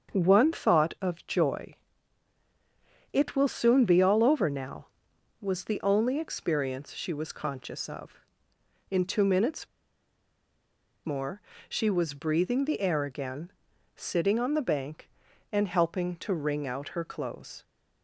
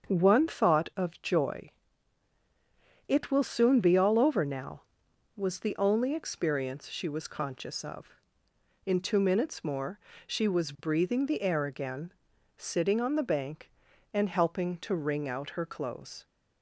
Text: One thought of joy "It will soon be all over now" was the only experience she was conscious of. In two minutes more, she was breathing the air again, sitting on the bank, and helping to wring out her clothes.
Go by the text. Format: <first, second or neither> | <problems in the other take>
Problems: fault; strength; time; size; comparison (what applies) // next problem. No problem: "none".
second | starts louder than the rest; strong; until 1.1 s; 7 dB; strong in the second // pauses between "joy" and "It"; strong; at 1.7 s; 1.3 s long; strong in the second // pauses between "minutes" and "more"; strong; at 9.6 s; 1.3 s long